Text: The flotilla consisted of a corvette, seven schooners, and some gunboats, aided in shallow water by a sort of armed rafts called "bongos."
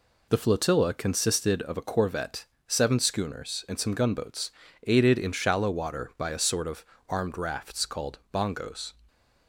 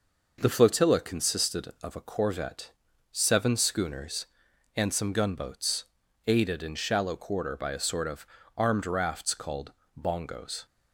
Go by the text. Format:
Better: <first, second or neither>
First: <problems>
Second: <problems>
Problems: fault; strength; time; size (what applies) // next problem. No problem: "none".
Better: first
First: pauses between "of" and "armed"; slight; at 6.8 s; 0.24 s long // pauses between "called" and "bongos"; slight; at 8.1 s; 0.16 s long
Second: says "quarter" for "water"; at 7.1 s // pauses between "of" and "armed"; slight; at 8.2 s; 0.30 s long // pauses between "called" and "bongos"; slight; at 9.7 s; 0.28 s long